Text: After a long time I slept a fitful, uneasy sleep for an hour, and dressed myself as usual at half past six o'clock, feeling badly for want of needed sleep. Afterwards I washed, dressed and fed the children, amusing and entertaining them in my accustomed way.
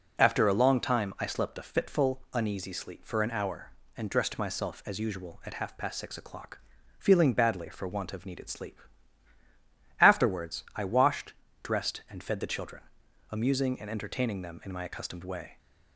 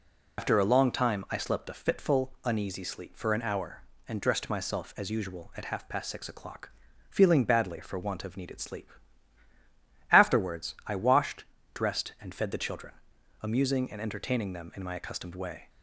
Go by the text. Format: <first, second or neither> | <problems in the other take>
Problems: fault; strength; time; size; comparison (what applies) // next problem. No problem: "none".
first | loses the start of "After"; at 0.3 s; 90 ms